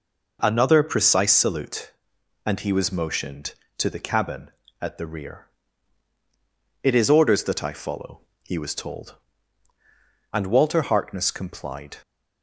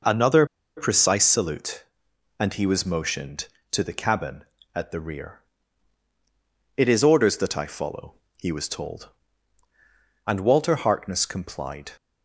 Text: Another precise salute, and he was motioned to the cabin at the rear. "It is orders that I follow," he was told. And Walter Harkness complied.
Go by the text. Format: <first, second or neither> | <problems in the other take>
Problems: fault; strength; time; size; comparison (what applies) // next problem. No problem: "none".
first | pauses between "Another" and "precise"; slight; at 0.4 s; 0.31 s long